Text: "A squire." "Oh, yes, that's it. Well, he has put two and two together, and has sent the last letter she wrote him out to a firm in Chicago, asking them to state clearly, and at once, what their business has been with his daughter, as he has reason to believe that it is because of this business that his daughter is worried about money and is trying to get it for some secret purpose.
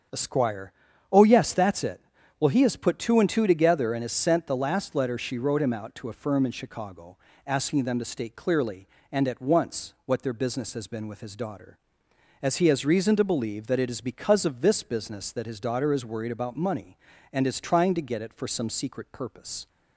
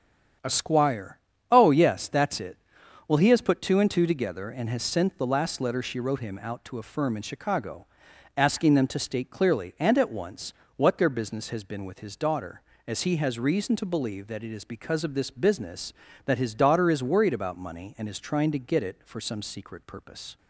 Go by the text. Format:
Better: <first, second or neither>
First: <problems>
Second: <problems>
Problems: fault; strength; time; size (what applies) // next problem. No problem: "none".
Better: neither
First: starts louder than the rest; strong; until 1.5 s; 8 dB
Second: starts louder than the rest; strong; until 1.7 s; 8.5 dB